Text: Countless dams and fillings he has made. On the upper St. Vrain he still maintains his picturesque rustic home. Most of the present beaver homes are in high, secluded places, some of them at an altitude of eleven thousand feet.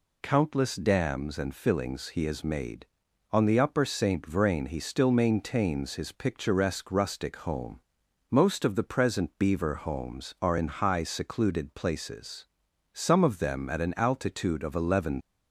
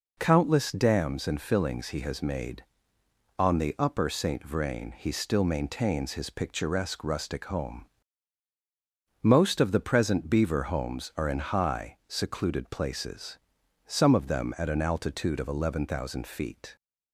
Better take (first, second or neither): second